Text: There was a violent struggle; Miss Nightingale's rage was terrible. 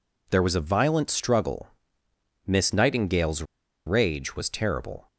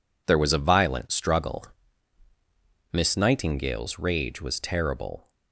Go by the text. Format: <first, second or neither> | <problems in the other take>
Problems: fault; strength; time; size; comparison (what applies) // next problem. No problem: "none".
second | pauses between "Nightingale's" and "rage"; at 3.4 s; 0.42 s long